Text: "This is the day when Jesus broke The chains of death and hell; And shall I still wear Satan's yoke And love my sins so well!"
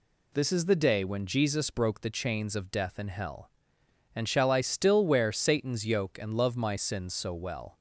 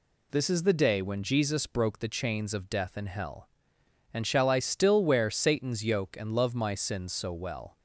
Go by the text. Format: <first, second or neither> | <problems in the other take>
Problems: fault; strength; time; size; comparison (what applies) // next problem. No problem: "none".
neither | none